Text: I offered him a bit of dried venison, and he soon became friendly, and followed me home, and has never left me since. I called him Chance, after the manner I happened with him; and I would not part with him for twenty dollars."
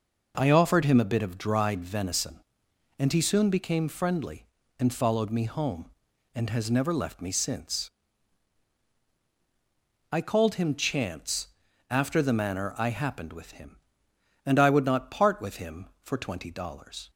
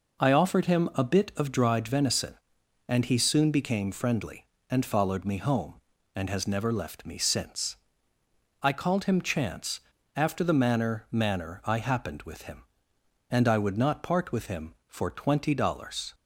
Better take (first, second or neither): first